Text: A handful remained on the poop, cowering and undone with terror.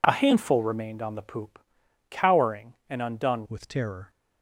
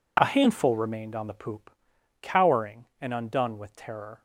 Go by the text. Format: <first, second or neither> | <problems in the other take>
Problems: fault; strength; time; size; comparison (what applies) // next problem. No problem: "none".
second | changes voice at "with"; from 3.4 s on; 0.6 s long